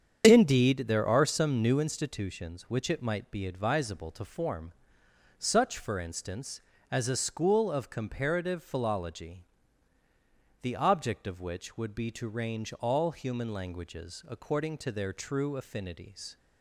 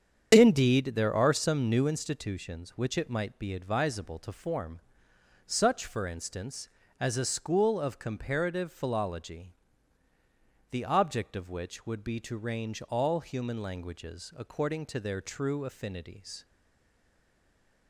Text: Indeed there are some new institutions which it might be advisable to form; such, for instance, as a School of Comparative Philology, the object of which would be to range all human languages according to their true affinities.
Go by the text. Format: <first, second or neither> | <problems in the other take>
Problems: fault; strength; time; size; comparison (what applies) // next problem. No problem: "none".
first | starts louder than the rest; strong; until 1.3 s; 7.5 dB; strong in the first // stays silent after the last word; noticeable; from 16.4 s on; 1.4 s long